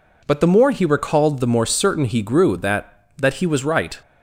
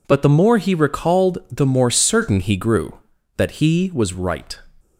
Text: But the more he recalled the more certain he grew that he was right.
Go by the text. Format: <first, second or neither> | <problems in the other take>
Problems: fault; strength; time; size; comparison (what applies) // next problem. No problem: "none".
second | says "that" twice; at 3.1 s